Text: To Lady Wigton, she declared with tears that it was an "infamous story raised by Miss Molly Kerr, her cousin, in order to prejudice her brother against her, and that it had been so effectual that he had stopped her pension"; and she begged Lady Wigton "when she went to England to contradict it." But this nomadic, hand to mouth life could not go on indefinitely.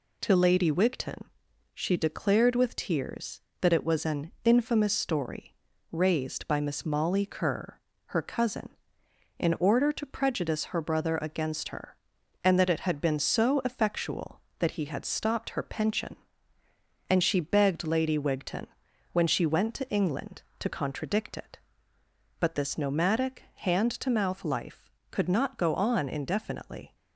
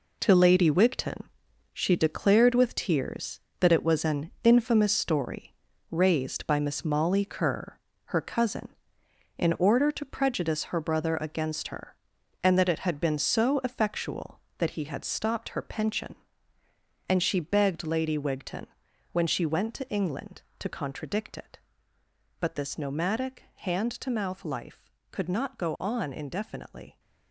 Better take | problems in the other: first | gets quieter; strong; throughout; 8.5 dB // pauses between "story" and "raised"; at 5.5 s; 0.38 s long; also in the first // pauses between "Wigton" and "when"; at 18.6 s; 0.44 s long; also in the first

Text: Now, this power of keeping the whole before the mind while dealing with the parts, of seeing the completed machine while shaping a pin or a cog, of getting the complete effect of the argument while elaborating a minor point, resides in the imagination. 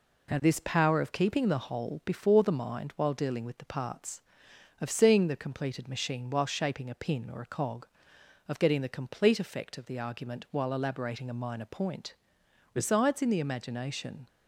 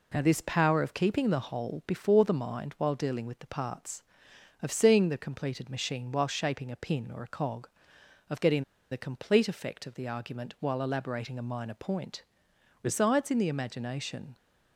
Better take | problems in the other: first | pauses between "getting" and "the"; slight; at 8.6 s; 0.28 s long

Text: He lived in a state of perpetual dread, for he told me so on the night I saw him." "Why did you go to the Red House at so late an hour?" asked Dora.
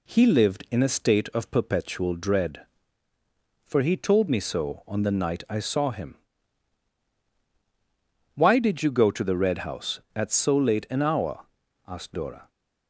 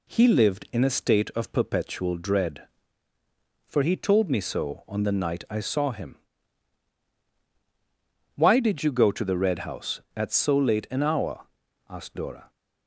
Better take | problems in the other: neither | none

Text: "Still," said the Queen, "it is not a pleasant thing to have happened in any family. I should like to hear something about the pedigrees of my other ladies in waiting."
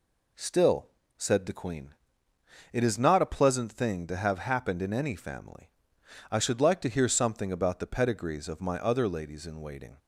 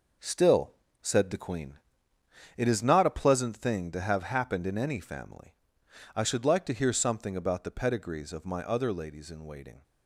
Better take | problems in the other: first | gets quieter; strong; throughout; 7.5 dB

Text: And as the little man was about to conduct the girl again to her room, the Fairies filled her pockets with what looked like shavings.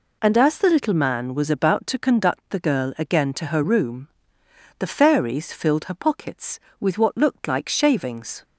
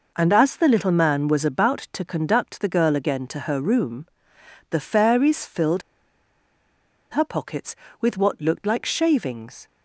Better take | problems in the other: first | pauses between "filled" and "her"; strong; at 5.8 s; 1.3 s long

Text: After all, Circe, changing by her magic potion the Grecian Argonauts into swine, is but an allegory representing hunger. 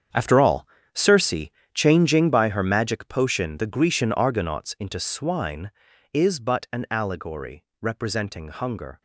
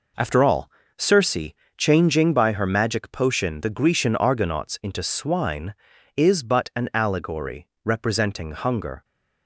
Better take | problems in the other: second | gets quieter; strong; throughout; 13 dB // pauses between "allegory" and "representing"; slight; at 7.6 s; 0.18 s long; slight in the second

